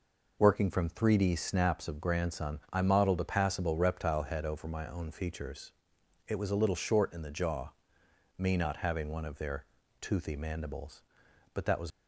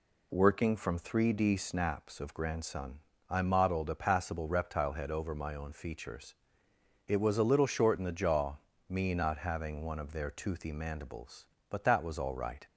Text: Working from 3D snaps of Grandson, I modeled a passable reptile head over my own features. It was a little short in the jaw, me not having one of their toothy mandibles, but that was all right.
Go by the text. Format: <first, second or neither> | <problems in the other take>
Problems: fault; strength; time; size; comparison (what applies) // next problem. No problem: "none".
second | pauses between "their" and "toothy"; slight; at 9.6 s; 0.36 s long // stops before "all right"; at 11.9 s